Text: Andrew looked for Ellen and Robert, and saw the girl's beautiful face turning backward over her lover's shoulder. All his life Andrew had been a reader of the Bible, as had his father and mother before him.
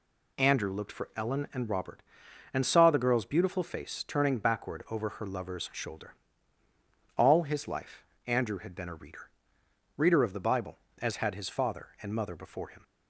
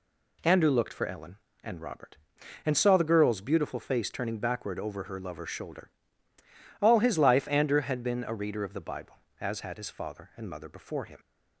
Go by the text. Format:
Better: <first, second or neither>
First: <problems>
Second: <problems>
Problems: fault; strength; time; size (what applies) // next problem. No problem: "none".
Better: second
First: pauses between "life" and "Andrew"; slight; at 8.0 s; 0.24 s long // says "reader" twice; at 9.9 s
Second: none